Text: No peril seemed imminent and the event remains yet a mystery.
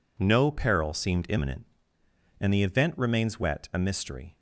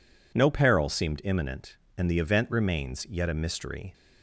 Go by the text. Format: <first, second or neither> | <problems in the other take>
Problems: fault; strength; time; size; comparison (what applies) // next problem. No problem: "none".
second | says "wet" for "yet"; at 3.3 s